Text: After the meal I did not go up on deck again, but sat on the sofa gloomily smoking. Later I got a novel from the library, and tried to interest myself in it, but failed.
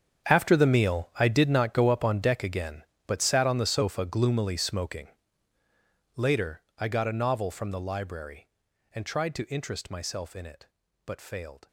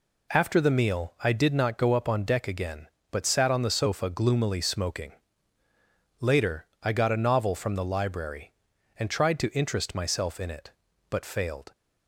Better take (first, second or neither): second